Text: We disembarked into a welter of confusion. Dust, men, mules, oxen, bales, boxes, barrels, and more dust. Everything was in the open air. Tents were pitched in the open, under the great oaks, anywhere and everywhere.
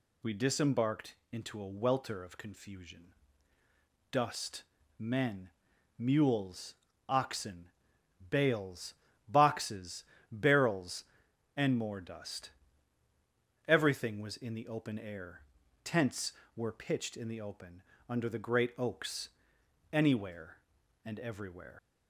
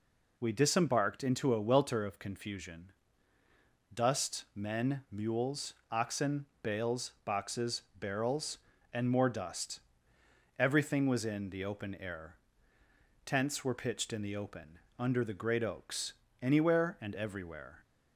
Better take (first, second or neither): second